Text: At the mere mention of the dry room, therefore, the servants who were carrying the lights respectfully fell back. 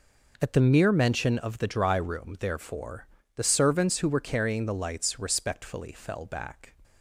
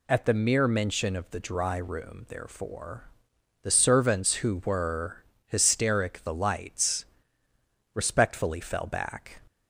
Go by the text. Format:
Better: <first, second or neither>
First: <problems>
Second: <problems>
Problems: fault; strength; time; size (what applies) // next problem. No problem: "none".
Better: first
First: none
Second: says "hysteric" for "carrying"; at 5.4 s // pauses between "lights" and "respectfully"; noticeable; at 7.0 s; 0.88 s long